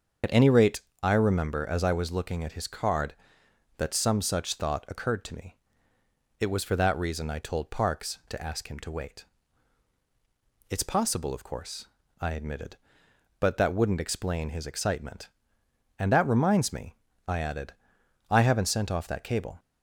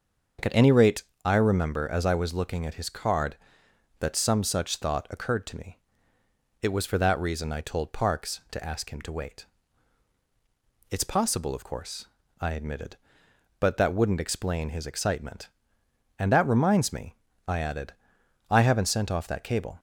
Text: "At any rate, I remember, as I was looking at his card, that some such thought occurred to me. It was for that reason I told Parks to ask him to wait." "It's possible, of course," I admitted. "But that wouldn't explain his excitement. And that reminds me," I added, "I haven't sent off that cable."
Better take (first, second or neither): second